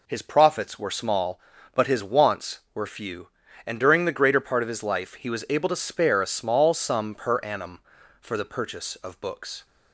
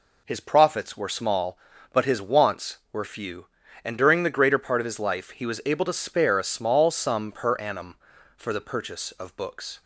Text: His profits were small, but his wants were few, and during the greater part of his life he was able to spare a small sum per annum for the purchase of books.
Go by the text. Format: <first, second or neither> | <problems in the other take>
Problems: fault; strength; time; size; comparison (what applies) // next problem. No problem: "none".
neither | none